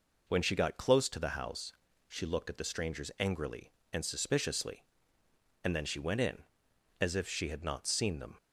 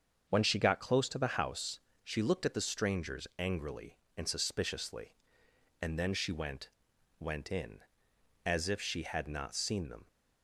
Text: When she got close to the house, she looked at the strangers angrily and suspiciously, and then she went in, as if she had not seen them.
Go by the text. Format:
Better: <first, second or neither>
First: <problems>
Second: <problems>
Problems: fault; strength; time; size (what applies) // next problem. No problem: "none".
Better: first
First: none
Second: starts louder than the rest; until 1.3 s; 7 dB // says "went" twice; at 7.1 s